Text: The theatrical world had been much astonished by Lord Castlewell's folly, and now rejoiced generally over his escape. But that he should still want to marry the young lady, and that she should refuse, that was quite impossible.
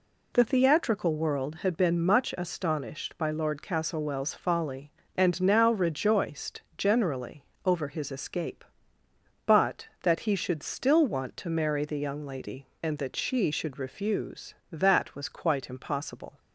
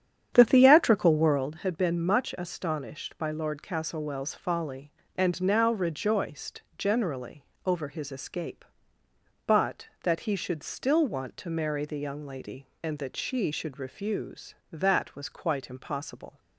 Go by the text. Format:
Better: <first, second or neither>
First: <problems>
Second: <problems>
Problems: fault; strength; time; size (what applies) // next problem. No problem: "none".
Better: first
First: pauses between "rejoiced" and "generally"; slight; at 6.6 s; 0.16 s long // pauses between "generally" and "over"; slight; at 7.4 s; 0.22 s long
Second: starts louder than the rest; strong; until 1.5 s; 9 dB // pauses between "rejoiced" and "generally"; slight; at 6.6 s; 0.16 s long // pauses between "generally" and "over"; slight; at 7.4 s; 0.22 s long